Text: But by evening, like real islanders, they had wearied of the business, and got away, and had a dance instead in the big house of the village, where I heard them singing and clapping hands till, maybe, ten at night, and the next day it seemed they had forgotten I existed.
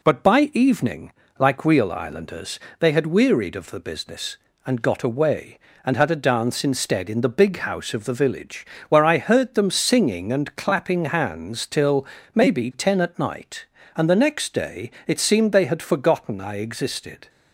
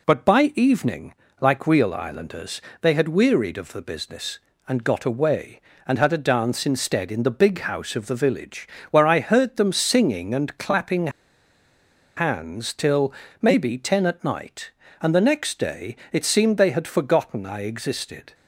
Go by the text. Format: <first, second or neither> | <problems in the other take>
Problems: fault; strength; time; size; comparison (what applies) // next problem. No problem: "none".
first | pauses between "clapping" and "hands"; at 11.0 s; 1.0 s long // pauses between "day" and "it"; slight; at 15.9 s; 0.16 s long; slight in the first